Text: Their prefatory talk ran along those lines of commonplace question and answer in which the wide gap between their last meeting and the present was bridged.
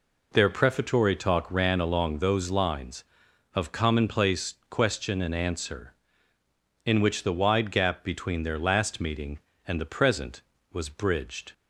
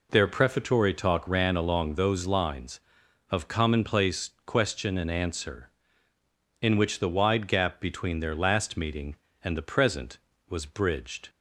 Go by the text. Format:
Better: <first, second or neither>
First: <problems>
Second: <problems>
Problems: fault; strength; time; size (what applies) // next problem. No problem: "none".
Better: neither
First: pauses between "commonplace" and "question"; slight; at 4.5 s; 0.16 s long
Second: pauses between "commonplace" and "question"; slight; at 4.2 s; 0.16 s long